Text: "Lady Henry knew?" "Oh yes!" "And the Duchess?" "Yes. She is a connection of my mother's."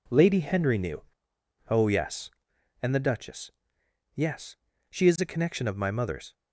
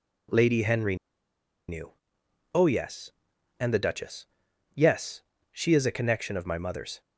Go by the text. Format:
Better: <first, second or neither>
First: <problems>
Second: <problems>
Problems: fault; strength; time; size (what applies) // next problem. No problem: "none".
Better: first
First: none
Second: pauses between "Henry" and "knew"; noticeable; at 0.9 s; 0.73 s long